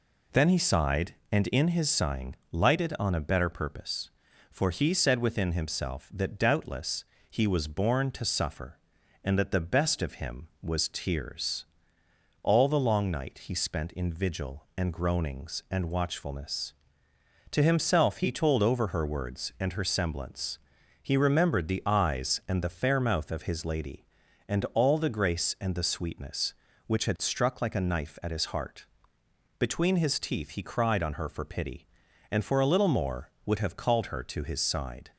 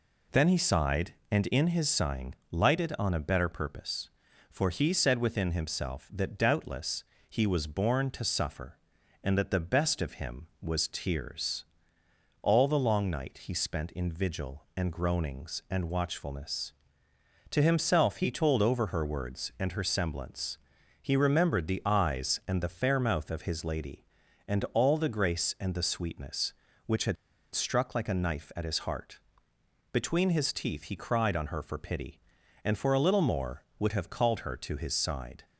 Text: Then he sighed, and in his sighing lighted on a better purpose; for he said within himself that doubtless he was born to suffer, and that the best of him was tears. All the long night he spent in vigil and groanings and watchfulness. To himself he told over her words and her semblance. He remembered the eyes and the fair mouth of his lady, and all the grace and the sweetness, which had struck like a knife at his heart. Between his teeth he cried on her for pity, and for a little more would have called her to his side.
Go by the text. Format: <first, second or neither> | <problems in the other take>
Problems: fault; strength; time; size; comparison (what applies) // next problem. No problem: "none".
first | pauses between "sighing" and "lighted"; slight; at 2.3 s; 0.16 s long; slight in the first // pauses between "doubtless" and "he"; slight; at 7.0 s; 0.24 s long; slight in the first // pauses between "had" and "struck"; at 27.1 s; 0.39 s long